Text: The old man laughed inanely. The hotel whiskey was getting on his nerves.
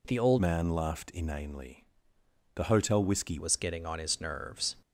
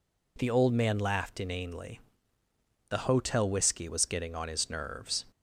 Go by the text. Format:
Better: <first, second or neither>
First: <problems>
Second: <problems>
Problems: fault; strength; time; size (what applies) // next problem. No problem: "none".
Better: second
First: changes voice from "man" to "whiskey"; from 0.4 to 3.3 s; 2.9 s long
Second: none